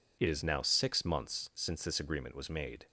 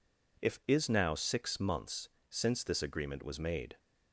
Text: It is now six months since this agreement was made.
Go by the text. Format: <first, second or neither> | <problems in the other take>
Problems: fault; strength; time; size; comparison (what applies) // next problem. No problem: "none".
first | says "If" for "It"; at 0.4 s // pauses between "months" and "since"; slight; at 2.0 s; 0.22 s long